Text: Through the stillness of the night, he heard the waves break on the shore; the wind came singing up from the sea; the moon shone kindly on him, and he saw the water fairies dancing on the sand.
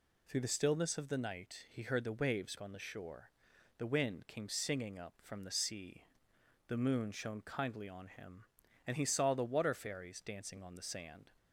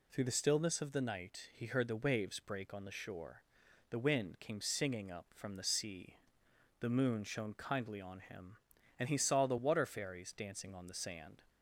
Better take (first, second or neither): second